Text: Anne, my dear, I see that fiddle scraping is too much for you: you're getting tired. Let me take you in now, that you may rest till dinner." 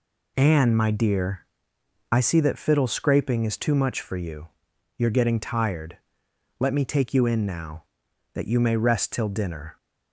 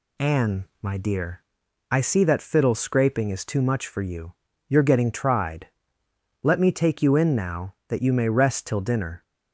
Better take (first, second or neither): first